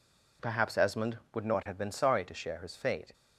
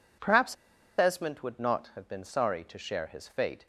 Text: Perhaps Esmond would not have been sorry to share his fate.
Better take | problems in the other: first | pauses between "Perhaps" and "Esmond"; at 0.5 s; 0.45 s long

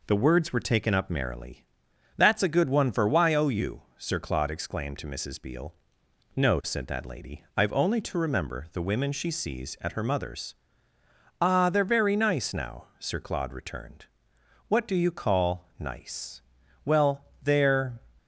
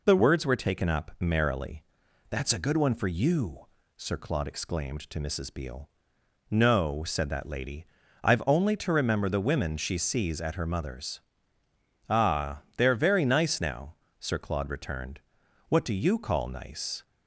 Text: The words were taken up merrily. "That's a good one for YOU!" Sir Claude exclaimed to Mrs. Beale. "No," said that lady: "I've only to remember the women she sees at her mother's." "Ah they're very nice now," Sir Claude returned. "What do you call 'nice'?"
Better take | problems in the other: second | goes on to say "Well they're"; noticeable; from 16.8 s on; 1.1 s long

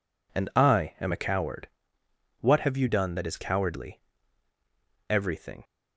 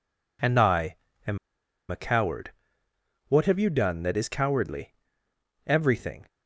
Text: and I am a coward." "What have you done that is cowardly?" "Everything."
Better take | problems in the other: first | pauses between "I" and "am"; slight; at 0.9 s; 0.30 s long // pauses between "am" and "a"; noticeable; at 1.3 s; 0.51 s long

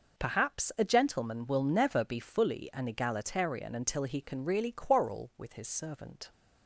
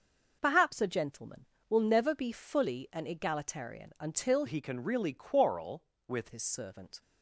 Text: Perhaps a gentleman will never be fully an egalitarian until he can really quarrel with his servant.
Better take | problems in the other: first | changes voice from "he" to "with"; from 4.4 to 6.2 s; 1.8 s long

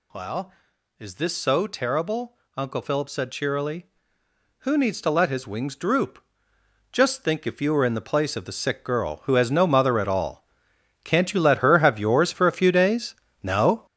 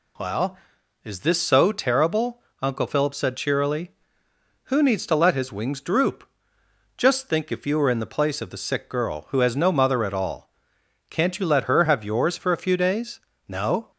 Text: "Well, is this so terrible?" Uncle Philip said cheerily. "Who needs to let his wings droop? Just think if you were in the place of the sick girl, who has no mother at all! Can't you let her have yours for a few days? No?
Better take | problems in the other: second | gets louder; strong; throughout; 8 dB

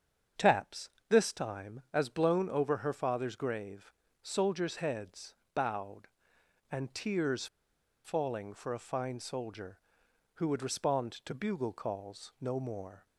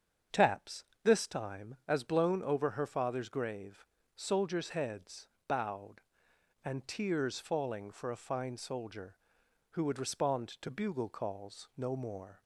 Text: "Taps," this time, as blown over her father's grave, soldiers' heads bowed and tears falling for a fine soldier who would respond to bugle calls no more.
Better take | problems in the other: second | starts louder than the rest; strong; until 1.5 s; 7.5 dB; strong in the second // pauses between "heads" and "bowed"; slight; at 5.3 s; 0.20 s long; slight in the second // pauses between "tears" and "falling"; noticeable; at 7.4 s; 0.58 s long

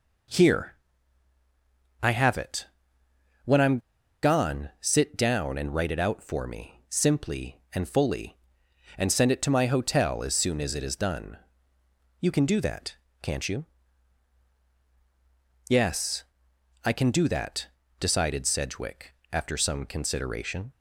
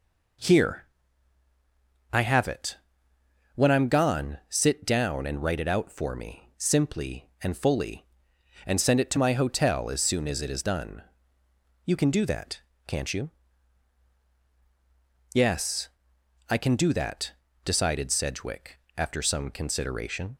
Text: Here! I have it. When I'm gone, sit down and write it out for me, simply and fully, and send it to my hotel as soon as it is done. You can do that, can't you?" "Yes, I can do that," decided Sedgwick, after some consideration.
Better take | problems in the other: second | pauses between "I'm" and "gone"; at 3.7 s; 0.43 s long

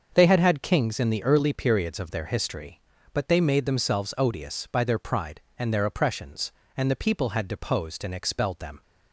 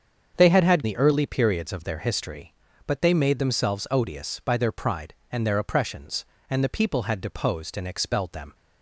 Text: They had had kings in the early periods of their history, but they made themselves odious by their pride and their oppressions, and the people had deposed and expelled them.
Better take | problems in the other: first | starts louder than the rest; until 1.3 s; 7 dB; also in the first // skips "kings in"; at 0.8 s

